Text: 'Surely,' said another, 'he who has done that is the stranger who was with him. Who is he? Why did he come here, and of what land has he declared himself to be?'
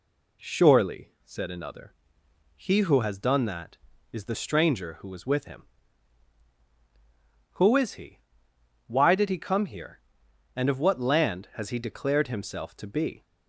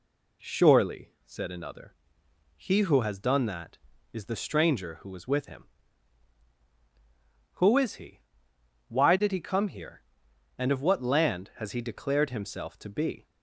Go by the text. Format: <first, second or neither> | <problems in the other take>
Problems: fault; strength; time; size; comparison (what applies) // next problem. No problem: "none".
neither | none